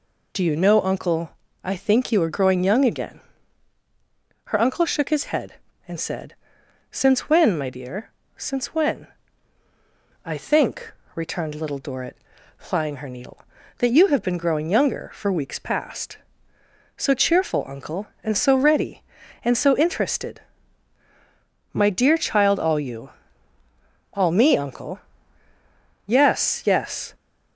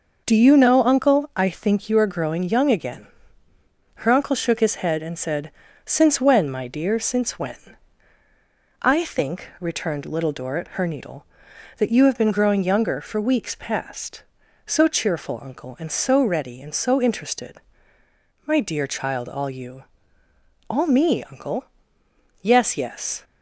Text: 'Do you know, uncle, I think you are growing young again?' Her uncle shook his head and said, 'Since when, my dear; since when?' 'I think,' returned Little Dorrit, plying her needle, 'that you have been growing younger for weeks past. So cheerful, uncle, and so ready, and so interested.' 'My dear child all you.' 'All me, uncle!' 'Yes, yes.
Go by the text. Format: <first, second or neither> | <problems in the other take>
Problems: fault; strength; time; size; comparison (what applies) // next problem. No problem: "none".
first | skips "plying"; at 10.7 s